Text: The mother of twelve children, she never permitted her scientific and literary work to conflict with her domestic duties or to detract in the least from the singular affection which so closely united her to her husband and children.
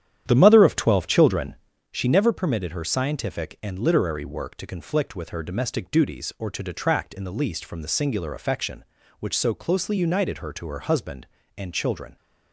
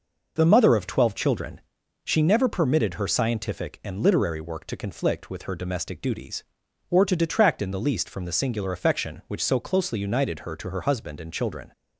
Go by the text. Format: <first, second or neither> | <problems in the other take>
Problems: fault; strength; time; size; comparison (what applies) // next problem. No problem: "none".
second | starts louder than the rest; strong; until 2.0 s; 10.5 dB